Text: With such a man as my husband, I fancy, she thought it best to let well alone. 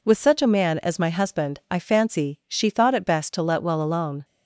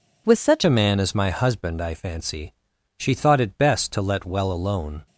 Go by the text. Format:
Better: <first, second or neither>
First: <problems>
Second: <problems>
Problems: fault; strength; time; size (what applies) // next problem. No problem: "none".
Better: first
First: none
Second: changes voice at "a"; from 0.6 s on; 4.4 s long